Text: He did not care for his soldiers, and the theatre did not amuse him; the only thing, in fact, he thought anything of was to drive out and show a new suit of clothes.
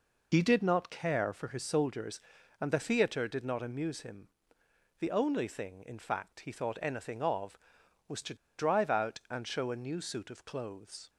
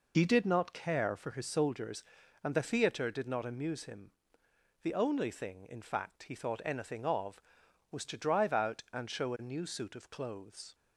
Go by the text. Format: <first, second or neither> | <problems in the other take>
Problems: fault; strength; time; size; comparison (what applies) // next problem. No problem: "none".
second | pauses between "to" and "drive"; slight; at 8.3 s; 0.22 s long